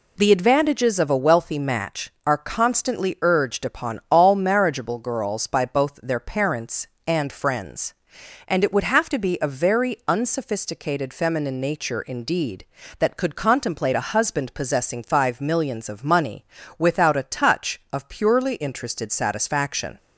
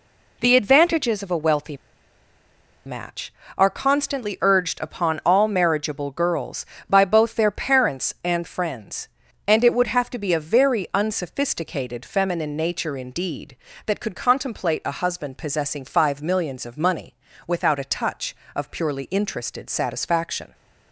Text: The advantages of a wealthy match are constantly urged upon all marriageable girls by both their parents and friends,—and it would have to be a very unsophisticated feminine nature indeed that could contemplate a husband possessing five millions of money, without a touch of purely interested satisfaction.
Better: first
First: none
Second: pauses between "wealthy" and "match"; at 1.7 s; 1.0 s long

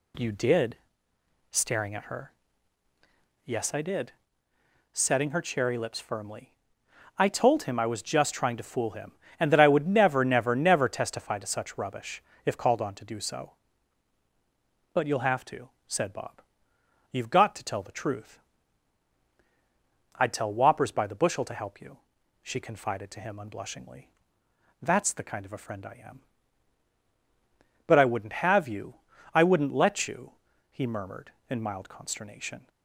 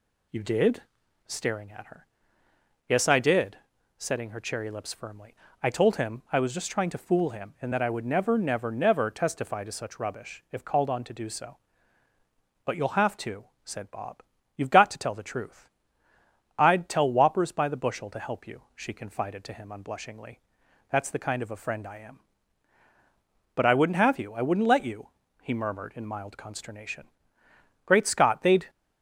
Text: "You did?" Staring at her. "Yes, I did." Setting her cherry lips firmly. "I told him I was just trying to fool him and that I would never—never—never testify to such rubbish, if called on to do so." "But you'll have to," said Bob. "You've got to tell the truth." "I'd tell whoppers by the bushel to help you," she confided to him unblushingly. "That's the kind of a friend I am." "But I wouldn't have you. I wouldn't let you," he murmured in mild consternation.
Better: first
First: none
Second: goes on to say "Great Scott they'd"; noticeable; from 27.8 s on; 0.84 s long

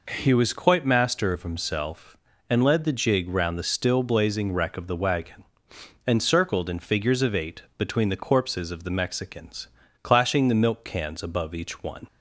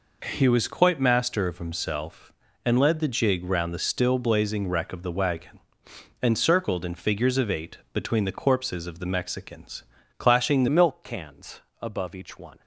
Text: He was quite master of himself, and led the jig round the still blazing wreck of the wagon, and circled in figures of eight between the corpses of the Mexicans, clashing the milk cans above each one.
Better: first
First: pauses between "eight" and "between"; slight; at 7.6 s; 0.16 s long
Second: pauses between "eight" and "between"; slight; at 7.7 s; 0.16 s long // changes voice at "milk"; from 10.6 s on; 2.0 s long // pauses between "cans" and "above"; slight; at 11.6 s; 0.18 s long

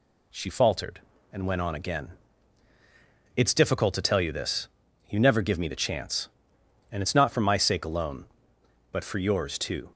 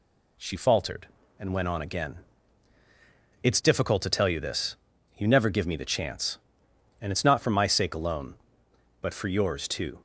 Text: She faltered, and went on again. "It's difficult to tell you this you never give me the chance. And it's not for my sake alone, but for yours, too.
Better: neither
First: pauses between "this" and "you"; at 4.6 s; 0.42 s long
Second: pauses between "this" and "you"; at 4.7 s; 0.42 s long

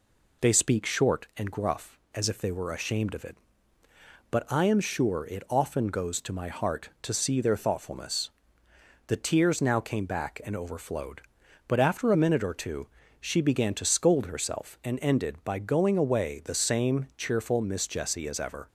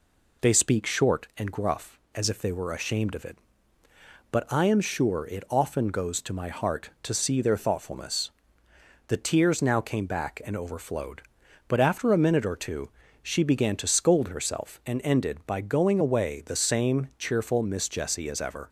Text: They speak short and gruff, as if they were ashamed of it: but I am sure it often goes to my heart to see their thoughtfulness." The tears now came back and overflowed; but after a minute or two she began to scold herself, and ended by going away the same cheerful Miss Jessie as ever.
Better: neither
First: pauses between "two" and "she"; slight; at 12.8 s; 0.34 s long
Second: pauses between "two" and "she"; slight; at 12.8 s; 0.34 s long

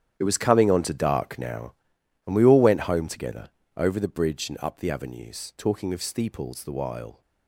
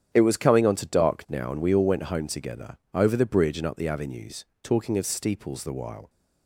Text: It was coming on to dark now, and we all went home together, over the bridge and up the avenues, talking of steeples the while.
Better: second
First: gets quieter; strong; throughout; 14.5 dB // starts louder than the rest; strong; until 1.2 s; 10 dB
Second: starts louder than the rest; strong; until 1.1 s; 9 dB

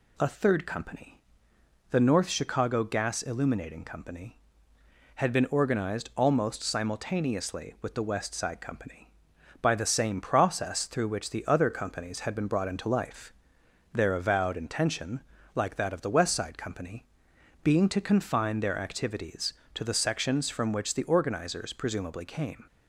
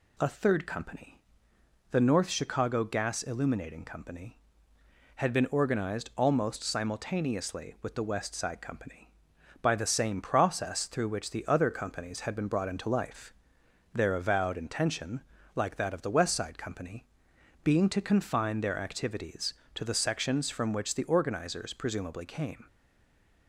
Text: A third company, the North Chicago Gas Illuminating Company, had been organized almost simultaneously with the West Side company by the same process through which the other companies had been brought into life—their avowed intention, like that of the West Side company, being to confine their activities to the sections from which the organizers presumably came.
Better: first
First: none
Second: stays silent after the last word; slight; from 22.6 s on; 0.8 s long

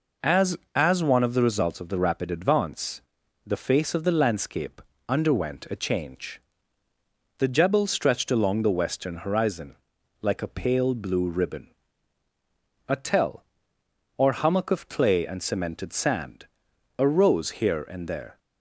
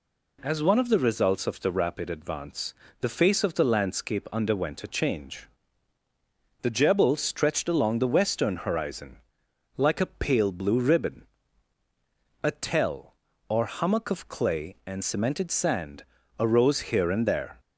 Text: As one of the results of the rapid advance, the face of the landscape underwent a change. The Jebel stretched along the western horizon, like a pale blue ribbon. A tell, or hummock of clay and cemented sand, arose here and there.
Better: second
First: says "As" twice; at 0.7 s // pauses between "landscape" and "underwent"; slight; at 4.8 s; 0.28 s long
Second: none

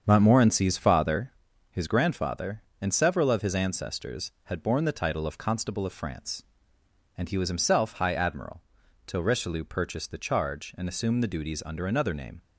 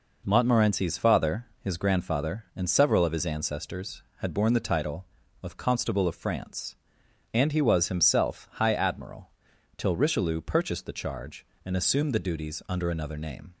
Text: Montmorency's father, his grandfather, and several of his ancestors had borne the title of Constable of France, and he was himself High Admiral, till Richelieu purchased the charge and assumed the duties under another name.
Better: second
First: starts louder than the rest; strong; until 1.2 s; 7 dB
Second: none

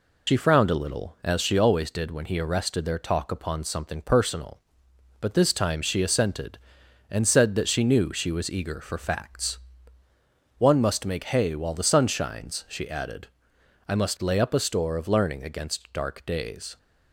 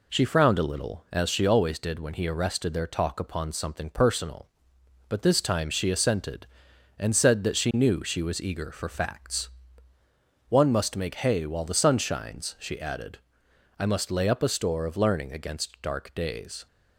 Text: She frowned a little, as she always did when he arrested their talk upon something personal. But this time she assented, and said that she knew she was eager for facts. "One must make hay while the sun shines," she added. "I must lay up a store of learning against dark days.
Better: second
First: loses the start of "She"; at 0.2 s; 35 ms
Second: none

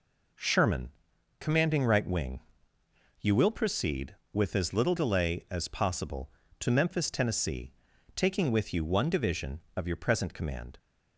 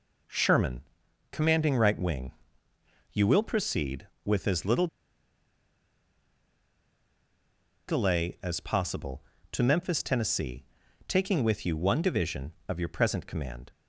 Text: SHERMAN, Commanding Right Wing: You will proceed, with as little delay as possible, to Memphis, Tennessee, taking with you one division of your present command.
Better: first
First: none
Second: pauses between "little" and "delay"; strong; at 4.8 s; 3.0 s long

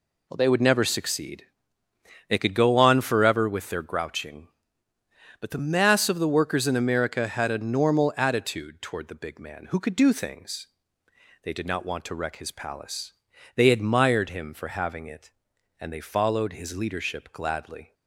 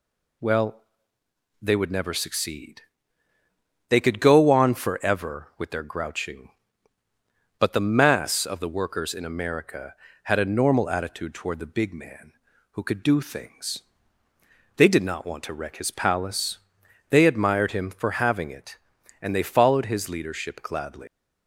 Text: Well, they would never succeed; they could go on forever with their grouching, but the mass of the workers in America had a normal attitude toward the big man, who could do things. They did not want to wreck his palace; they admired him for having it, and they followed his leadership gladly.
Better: first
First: none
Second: leaves "gladly" unfinished; at 21.0 s; 155 ms

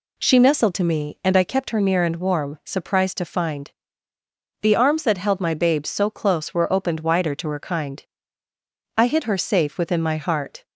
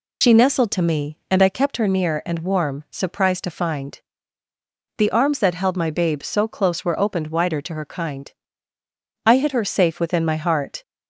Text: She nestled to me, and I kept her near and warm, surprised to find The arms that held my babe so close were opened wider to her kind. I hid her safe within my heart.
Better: first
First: pauses between "find" and "The"; noticeable; at 3.6 s; 0.92 s long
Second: loses the start of "She"; at 0.2 s; 80 ms // pauses between "find" and "The"; noticeable; at 4.0 s; 0.95 s long

